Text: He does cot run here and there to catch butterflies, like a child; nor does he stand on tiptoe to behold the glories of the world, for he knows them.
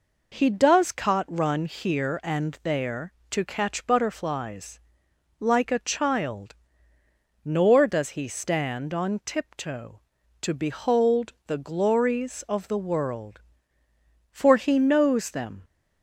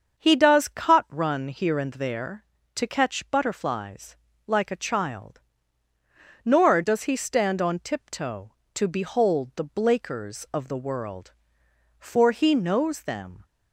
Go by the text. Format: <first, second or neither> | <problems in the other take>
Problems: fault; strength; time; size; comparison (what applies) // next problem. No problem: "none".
first | starts louder than the rest; until 1.2 s; 7 dB // says "blakers" for "glories"; at 9.6 s